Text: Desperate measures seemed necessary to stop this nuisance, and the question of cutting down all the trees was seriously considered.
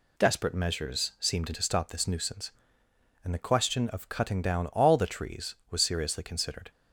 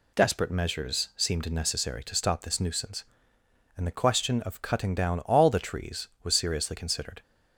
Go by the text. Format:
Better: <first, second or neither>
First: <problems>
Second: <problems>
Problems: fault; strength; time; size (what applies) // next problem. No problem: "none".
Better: second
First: skips "necessary"; at 1.5 s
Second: none